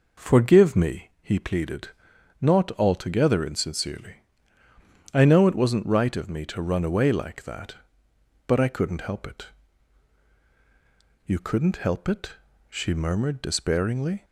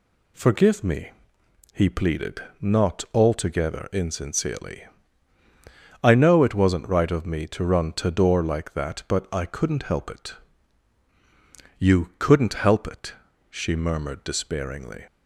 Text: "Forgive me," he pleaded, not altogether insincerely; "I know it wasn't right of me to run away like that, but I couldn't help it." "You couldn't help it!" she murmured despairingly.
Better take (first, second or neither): first